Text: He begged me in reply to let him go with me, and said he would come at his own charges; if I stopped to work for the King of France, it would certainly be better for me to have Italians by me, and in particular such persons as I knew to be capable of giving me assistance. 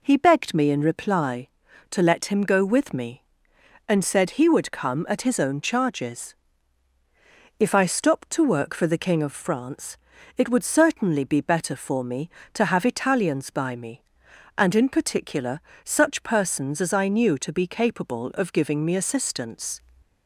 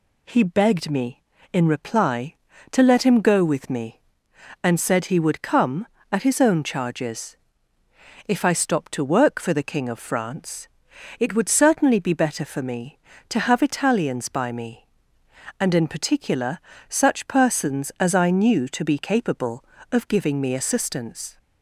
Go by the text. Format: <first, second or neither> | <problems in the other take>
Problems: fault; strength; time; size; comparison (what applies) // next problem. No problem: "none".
neither | pauses between "particular" and "such"; slight; the same in both